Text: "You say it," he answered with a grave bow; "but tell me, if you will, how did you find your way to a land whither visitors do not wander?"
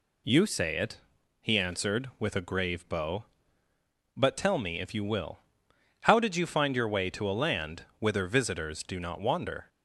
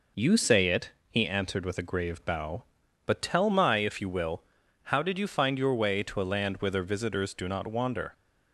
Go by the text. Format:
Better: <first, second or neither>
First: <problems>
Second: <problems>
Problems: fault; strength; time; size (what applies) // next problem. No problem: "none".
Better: first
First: none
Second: says "my" for "me"; at 3.4 s